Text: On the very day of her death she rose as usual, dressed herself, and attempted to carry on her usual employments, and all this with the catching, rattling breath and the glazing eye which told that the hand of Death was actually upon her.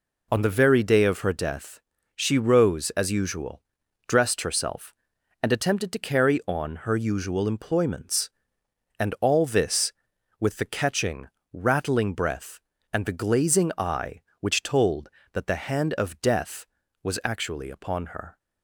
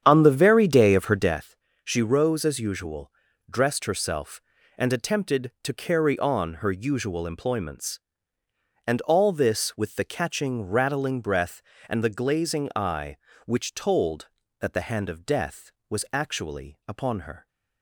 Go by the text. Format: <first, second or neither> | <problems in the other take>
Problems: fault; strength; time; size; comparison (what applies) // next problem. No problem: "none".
first | starts louder than the rest; strong; until 1.5 s; 9 dB // pauses between "death" and "she"; slight; at 1.5 s; 0.30 s long; slight in the first